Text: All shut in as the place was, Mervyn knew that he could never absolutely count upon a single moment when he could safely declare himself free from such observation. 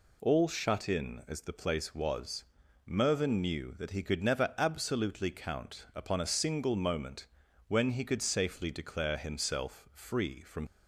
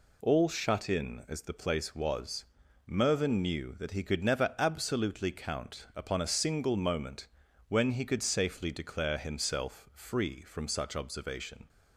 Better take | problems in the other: second | pauses between "moment" and "when"; at 7.2 s; 0.42 s long; also in the second // stops before "such observation"; at 10.6 s

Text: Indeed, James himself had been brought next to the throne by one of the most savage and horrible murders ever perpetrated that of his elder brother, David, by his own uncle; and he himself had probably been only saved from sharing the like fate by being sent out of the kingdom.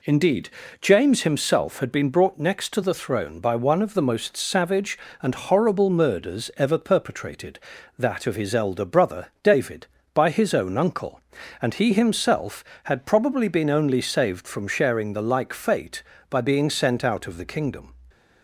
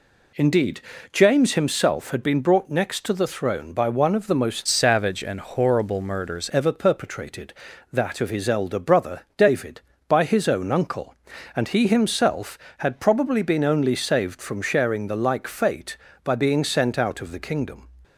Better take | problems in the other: first | changes voice from "savage" to "murders"; from 4.6 to 6.5 s; 1.9 s long

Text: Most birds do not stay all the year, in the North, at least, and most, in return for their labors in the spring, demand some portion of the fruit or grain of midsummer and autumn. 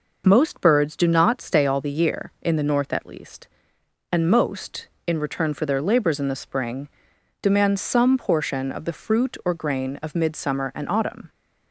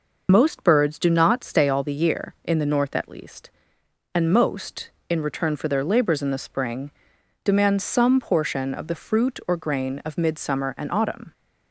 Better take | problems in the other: first | loses the start of "Most"; at 0.2 s; 25 ms

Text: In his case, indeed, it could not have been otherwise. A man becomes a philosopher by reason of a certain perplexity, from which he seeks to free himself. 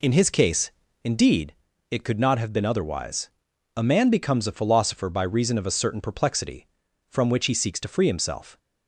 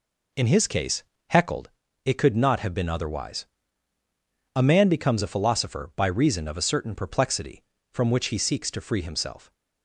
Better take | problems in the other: first | says "heckled" for "indeed"; at 1.2 s

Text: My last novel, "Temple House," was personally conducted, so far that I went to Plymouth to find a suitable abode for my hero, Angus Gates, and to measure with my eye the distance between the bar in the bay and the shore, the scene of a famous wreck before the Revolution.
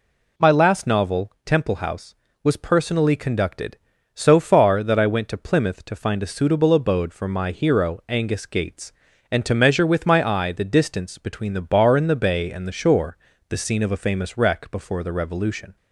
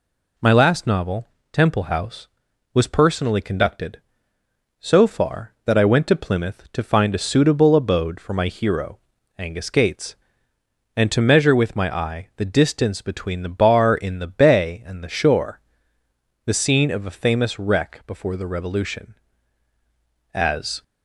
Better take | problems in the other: first | goes on to say "As"; slight; from 20.3 s on; 0.48 s long

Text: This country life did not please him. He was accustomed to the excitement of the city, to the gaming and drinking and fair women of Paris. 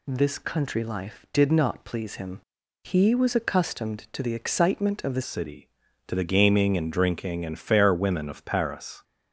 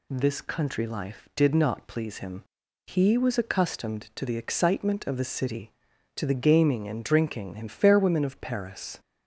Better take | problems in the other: second | changes voice at "city"; from 5.2 s on; 3.8 s long

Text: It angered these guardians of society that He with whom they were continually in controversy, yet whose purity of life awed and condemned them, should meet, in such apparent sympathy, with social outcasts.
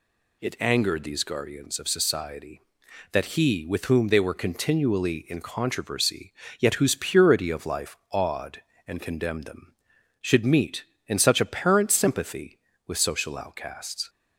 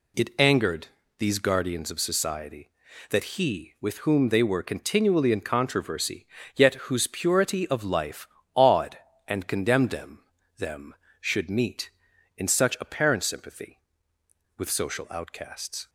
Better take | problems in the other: first | pauses between "angered" and "these"; slight; at 0.8 s; 0.30 s long // pauses between "life" and "awed"; slight; at 8.2 s; 0.26 s long; slight in the first // says "them" twice; at 10.5 s

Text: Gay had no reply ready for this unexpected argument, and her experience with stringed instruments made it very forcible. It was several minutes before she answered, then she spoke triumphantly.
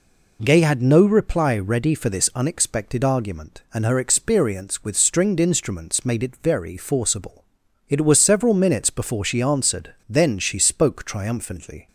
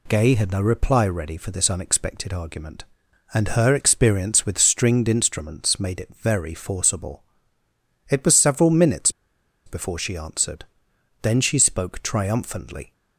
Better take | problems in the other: first | pauses between "minutes" and "before"; noticeable; at 9.1 s; 0.55 s long

